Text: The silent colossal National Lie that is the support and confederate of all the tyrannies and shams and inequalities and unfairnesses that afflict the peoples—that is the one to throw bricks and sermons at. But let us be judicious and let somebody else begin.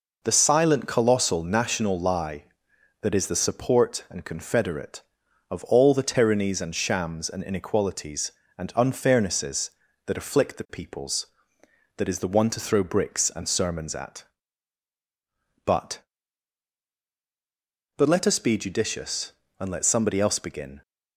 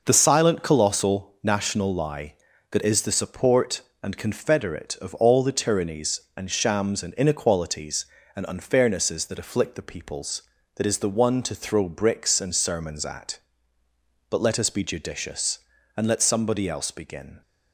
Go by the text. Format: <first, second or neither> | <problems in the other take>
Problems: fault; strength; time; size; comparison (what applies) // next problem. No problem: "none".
second | says "But" twice; at 17.9 s